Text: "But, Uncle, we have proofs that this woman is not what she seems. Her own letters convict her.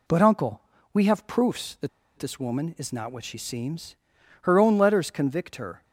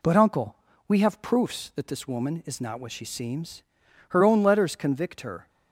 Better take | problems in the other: second | pauses between "that" and "this"; slight; at 1.8 s; 0.28 s long

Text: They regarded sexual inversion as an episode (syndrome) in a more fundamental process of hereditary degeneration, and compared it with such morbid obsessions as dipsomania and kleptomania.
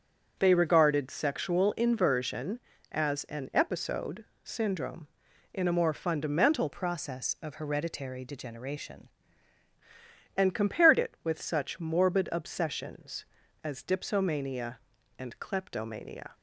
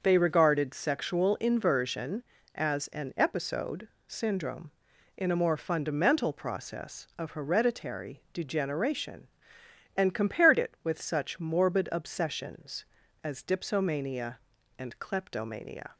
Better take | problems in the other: second | starts louder than the rest; until 1.4 s; 7 dB; noticeable in the second // changes voice from "process" to "degeneration"; from 6.7 to 9.0 s; 2.3 s long

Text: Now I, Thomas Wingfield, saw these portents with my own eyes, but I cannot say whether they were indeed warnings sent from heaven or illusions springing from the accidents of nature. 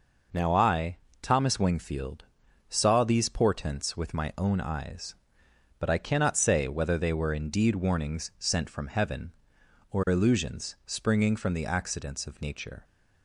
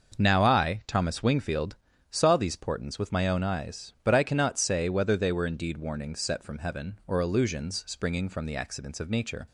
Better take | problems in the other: first | starts louder than the rest; noticeable; until 1.2 s; 6 dB // says "set" for "sent"; at 6.1 s

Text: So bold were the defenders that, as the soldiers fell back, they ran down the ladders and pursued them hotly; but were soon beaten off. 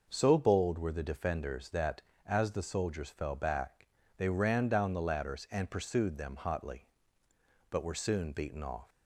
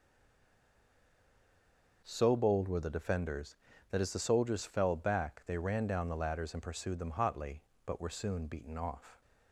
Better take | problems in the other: first | stays silent before the first word; noticeable; until 2.0 s; 2.0 s long

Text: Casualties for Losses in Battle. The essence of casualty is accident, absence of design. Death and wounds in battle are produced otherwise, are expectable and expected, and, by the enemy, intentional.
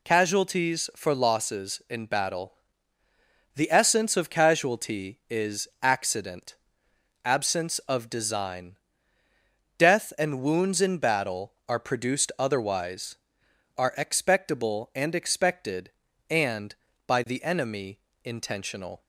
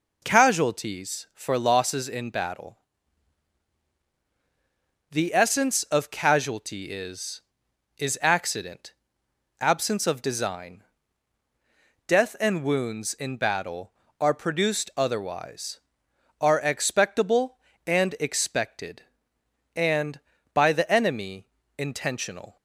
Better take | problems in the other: first | says "is" twice; at 7.9 s

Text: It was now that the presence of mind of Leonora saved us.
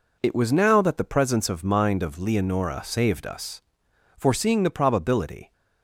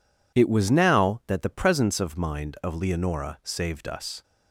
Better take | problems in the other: second | goes on to say "Foreseeing the probability"; from 4.1 s on; 1.3 s long

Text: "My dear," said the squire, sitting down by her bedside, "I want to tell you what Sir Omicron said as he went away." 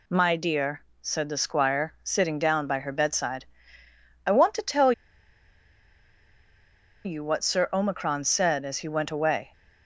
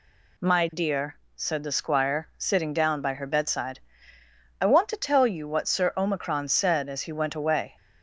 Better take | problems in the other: second | pauses between "tell" and "you"; strong; at 4.9 s; 2.1 s long

